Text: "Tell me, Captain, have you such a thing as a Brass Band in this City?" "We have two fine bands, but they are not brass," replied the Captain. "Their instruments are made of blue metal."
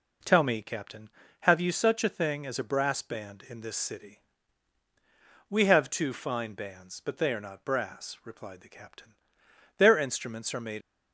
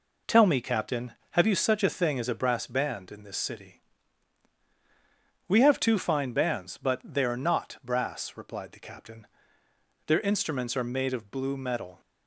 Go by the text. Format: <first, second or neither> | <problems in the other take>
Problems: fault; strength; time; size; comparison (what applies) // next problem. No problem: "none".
second | stops before "of blue metal"; at 10.8 s